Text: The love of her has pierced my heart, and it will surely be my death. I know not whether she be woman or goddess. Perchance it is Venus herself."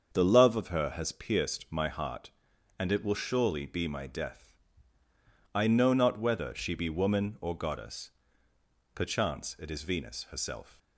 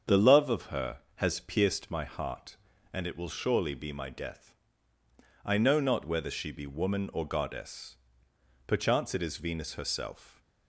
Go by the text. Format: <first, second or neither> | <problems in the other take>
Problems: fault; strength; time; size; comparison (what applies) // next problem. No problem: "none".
neither | starts louder than the rest; the same in both